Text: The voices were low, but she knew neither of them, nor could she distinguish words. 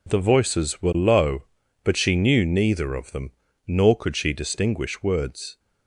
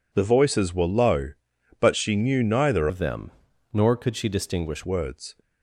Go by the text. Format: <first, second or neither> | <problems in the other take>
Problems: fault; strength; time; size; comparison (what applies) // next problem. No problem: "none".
first | changes voice from "of" to "distinguish"; from 2.8 to 4.8 s; 2.0 s long